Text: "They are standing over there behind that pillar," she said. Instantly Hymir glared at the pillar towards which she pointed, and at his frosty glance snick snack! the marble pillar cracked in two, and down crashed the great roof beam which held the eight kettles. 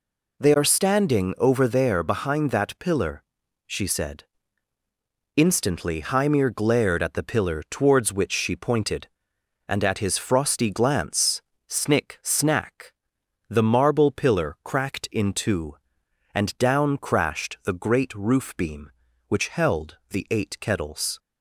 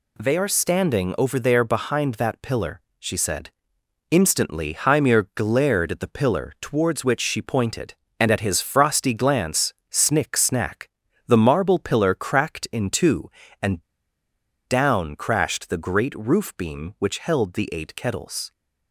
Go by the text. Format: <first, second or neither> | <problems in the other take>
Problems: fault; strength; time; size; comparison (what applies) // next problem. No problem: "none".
first | pauses between "glance" and "snick"; slight; at 9.7 s; 0.16 s long; slight in the first // pauses between "and" and "down"; noticeable; at 13.8 s; 0.83 s long